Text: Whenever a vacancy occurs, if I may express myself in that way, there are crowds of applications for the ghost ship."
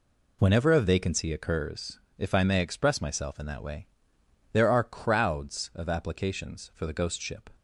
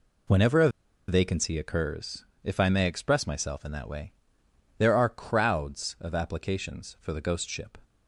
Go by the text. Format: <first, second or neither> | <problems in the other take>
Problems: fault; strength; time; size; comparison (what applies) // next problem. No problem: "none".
first | pauses between "a" and "vacancy"; at 0.6 s; 0.39 s long